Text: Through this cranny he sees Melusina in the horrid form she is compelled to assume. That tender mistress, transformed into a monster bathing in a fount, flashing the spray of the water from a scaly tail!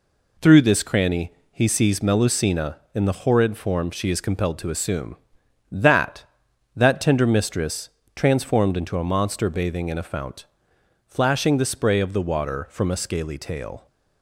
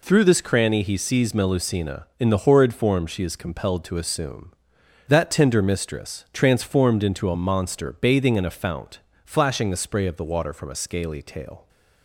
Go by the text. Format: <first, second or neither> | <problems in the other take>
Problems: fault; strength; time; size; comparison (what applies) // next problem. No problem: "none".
second | pauses between "cranny" and "he"; slight; at 1.3 s; 0.20 s long // says "That" twice; at 6.7 s